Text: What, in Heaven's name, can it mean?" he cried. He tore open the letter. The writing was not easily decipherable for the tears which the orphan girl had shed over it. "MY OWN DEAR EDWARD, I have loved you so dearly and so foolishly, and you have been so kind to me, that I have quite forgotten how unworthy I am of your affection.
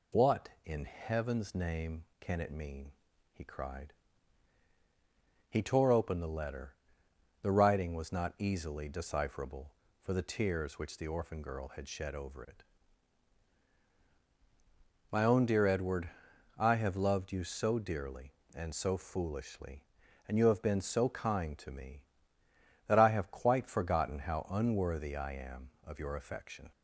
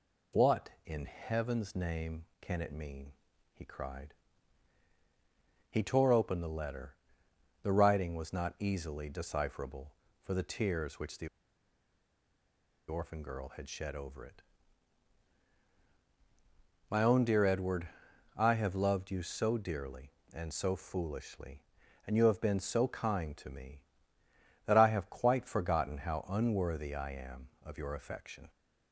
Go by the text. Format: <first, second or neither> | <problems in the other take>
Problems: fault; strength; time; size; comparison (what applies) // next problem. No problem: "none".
first | pauses between "the" and "orphan"; strong; at 11.2 s; 1.6 s long